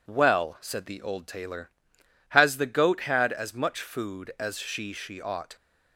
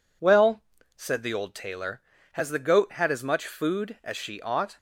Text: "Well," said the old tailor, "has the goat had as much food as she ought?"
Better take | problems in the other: second | says "she" twice; at 4.9 s

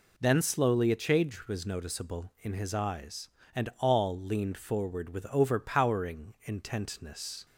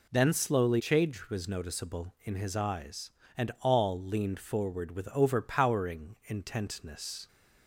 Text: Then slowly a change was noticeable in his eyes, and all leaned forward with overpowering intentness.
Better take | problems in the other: first | skips "a"; at 0.7 s

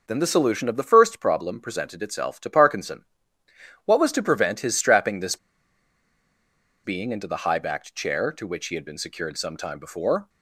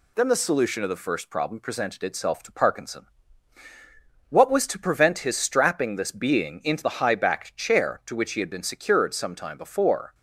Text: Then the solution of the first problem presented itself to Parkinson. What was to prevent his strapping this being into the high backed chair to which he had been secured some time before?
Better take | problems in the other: second | pauses between "this" and "being"; strong; at 5.3 s; 1.4 s long

